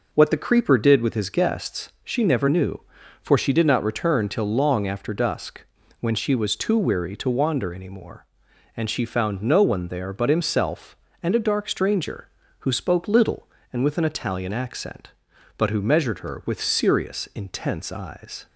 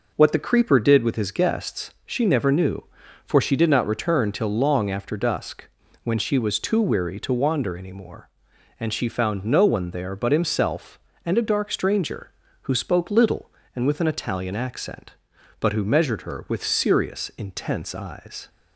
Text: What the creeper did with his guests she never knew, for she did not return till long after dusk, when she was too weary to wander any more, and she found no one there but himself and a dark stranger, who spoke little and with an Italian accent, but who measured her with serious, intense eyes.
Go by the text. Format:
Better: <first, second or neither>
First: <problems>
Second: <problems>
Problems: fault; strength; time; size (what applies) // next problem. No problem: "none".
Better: neither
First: none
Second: none